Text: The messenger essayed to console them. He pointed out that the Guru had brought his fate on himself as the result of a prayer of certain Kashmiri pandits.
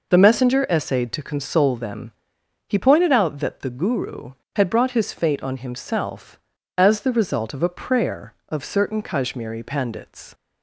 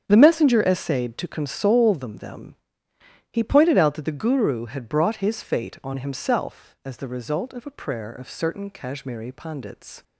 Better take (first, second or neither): first